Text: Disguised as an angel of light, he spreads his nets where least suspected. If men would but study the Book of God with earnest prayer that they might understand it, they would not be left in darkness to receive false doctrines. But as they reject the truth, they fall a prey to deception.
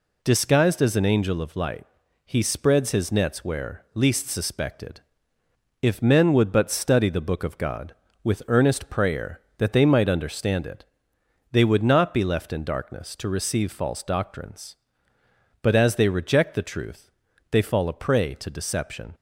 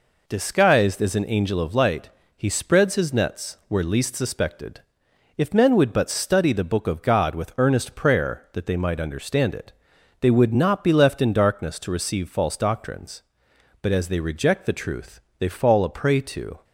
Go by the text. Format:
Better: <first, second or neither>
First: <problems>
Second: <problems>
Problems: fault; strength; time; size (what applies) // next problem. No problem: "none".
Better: first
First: none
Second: stops before "deception"; at 16.6 s